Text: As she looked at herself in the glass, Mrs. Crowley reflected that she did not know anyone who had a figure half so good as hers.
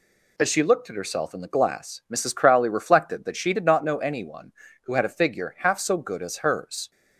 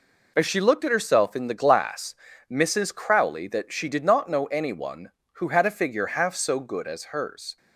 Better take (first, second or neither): first